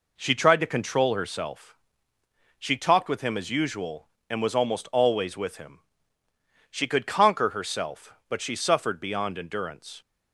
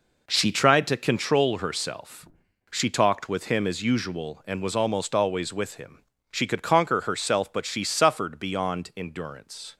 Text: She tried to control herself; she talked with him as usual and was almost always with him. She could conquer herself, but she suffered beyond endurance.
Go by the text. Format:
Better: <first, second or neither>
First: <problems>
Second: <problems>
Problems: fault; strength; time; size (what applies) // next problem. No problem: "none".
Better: first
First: none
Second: gets quieter; strong; throughout; 8.5 dB